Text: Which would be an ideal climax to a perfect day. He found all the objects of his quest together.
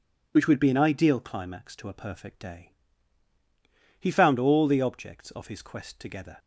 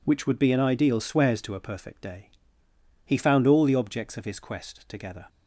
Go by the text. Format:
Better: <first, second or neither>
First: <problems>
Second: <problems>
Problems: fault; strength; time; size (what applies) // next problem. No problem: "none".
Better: first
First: none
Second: says "swears" for "climax"; at 0.9 s